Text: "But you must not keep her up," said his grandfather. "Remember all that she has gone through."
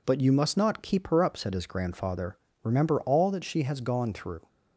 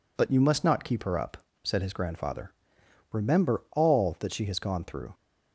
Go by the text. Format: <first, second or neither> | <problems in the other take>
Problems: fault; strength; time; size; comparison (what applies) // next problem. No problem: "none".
neither | none